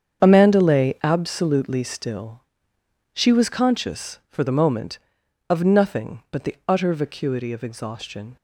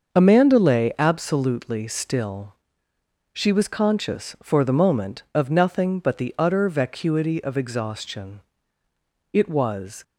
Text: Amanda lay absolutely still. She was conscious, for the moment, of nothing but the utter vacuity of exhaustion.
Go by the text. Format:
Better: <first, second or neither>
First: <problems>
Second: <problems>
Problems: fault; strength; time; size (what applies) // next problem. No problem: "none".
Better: first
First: starts louder than the rest; strong; until 1.2 s; 7.5 dB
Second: starts louder than the rest; until 1.1 s; 6.5 dB // goes on to say "It was"; noticeable; from 9.3 s on; 0.70 s long